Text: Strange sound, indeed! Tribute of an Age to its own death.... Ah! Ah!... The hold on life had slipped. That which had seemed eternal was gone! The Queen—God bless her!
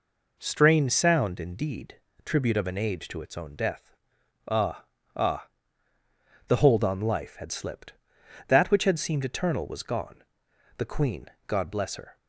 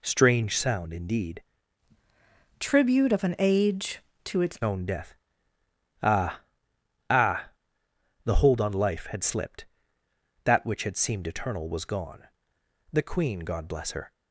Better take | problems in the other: first | changes voice from "Tribute" to "its"; from 2.5 to 4.5 s; 2.0 s long

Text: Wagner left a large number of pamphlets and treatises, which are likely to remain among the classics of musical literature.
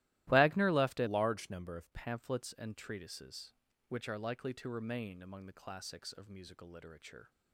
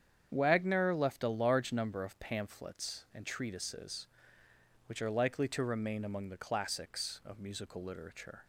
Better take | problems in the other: second | starts louder than the rest; strong; until 1.3 s; 16.5 dB; strong in the second // changes voice from "large" to "of"; from 1.0 to 1.9 s; 0.9 s long

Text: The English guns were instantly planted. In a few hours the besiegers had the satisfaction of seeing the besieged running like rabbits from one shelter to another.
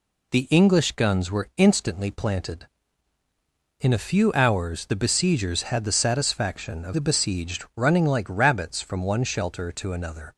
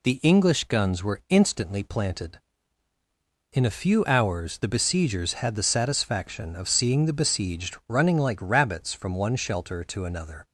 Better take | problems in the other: second | skips "seeing"; at 6.9 s

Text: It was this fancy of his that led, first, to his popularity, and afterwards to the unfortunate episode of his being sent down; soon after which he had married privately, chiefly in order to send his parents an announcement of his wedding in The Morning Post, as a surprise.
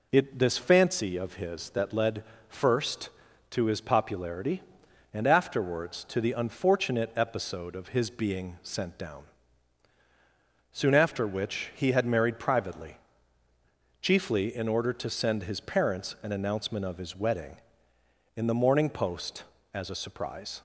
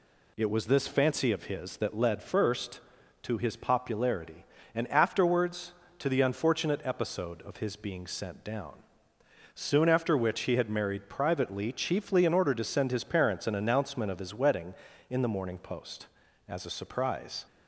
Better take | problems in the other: second | skips "was"; at 0.3 s

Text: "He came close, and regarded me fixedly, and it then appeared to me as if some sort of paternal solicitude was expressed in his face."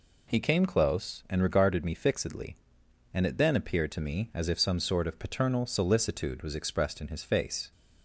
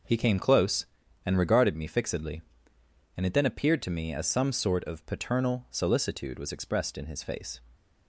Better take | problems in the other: first | skips "if"; at 4.2 s

